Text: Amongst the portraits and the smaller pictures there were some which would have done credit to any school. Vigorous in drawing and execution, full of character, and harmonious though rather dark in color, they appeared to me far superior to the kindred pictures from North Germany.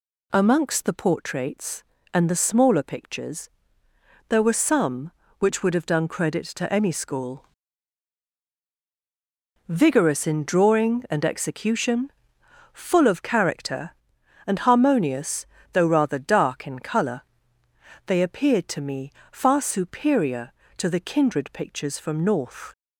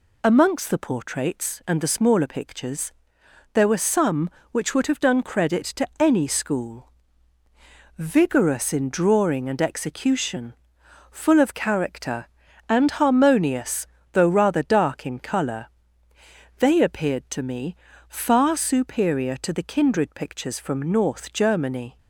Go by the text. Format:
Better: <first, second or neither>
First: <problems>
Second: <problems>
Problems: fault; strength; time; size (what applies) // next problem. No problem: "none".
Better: second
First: pauses between "pictures" and "there"; noticeable; at 3.4 s; 0.78 s long // pauses between "harmonious" and "though"; slight; at 15.4 s; 0.26 s long // pauses between "me" and "far"; slight; at 19.0 s; 0.22 s long // stops before "Germany"; at 22.7 s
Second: pauses between "pictures" and "there"; noticeable; at 2.9 s; 0.62 s long // pauses between "harmonious" and "though"; slight; at 13.8 s; 0.28 s long // pauses between "me" and "far"; slight; at 17.7 s; 0.32 s long